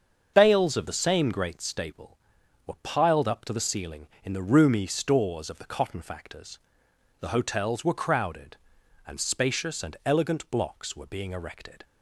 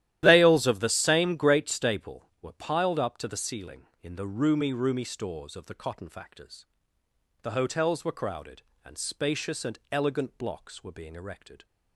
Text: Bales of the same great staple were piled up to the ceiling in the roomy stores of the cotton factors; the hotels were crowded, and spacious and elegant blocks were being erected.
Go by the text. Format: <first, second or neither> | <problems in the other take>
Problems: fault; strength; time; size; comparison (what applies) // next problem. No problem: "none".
first | starts louder than the rest; strong; until 1.2 s; 13 dB; also in the first // says "roomy" twice; at 4.7 s